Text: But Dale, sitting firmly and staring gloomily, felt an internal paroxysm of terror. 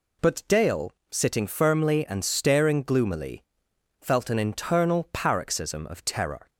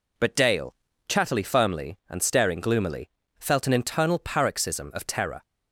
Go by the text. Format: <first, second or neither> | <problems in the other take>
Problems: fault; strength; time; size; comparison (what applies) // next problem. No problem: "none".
first | says "chattily" for "sitting"; at 1.0 s